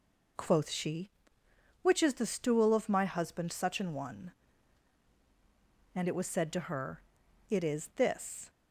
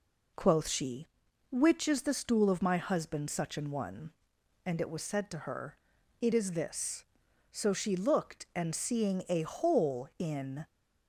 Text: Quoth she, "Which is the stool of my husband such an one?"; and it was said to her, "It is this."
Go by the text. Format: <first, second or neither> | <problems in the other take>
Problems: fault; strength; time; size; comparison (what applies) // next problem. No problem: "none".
first | goes on to say "So she looked and seeing a hole in"; strong; from 7.5 s on; 3.1 s long